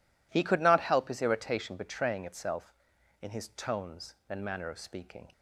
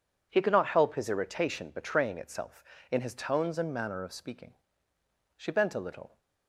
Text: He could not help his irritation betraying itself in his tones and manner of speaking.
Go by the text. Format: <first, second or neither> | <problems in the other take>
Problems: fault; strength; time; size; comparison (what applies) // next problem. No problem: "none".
first | goes on to say "She bent a little"; noticeable; from 5.3 s on; 0.82 s long